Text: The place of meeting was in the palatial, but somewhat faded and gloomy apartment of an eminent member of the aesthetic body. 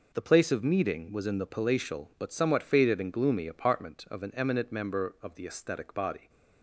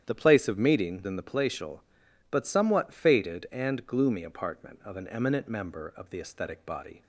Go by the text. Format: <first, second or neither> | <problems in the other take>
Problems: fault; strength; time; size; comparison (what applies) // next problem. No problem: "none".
first | starts louder than the rest; strong; until 1.0 s; 9.5 dB // skips "was"; at 1.0 s